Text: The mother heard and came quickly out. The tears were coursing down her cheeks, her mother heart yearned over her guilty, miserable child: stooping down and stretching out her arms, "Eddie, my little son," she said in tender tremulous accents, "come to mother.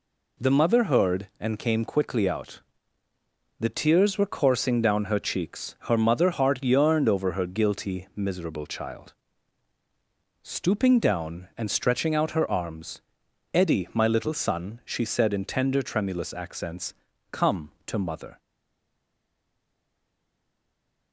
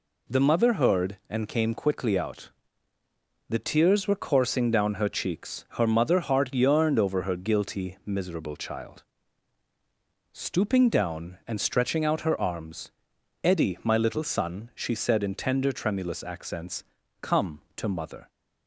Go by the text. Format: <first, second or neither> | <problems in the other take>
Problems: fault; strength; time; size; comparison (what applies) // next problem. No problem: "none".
second | stays silent after the last word; strong; from 18.3 s on; 2.8 s long